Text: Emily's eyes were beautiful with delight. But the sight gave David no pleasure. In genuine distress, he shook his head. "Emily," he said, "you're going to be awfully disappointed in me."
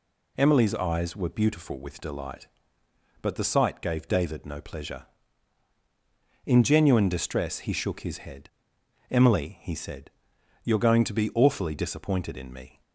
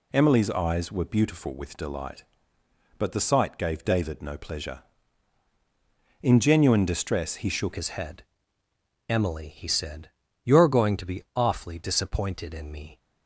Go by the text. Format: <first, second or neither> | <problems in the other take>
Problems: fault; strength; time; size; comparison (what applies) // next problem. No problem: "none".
first | changes voice at "his"; from 7.7 s on; 5.2 s long